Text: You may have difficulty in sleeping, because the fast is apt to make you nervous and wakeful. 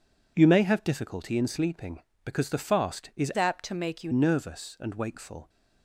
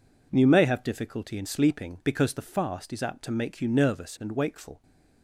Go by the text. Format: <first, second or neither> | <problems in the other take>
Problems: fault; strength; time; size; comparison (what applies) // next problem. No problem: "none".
second | changes voice from "apt" to "you"; from 3.3 to 4.1 s; 0.8 s long